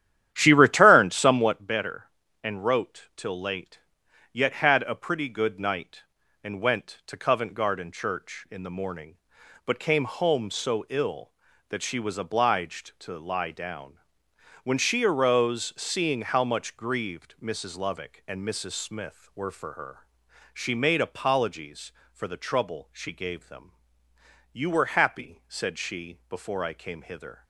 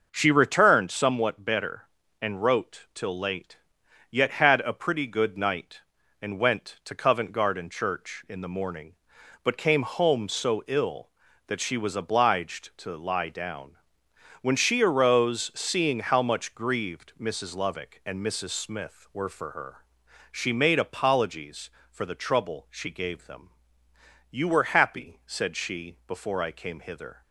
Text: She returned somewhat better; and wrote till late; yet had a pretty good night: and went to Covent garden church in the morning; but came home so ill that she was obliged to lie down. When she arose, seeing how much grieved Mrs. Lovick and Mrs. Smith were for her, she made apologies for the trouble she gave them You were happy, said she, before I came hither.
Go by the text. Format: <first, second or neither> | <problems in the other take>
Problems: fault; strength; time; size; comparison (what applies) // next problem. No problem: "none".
second | starts louder than the rest; strong; until 1.7 s; 11 dB // pauses between "them" and "You"; noticeable; at 23.7 s; 0.82 s long; noticeable in the second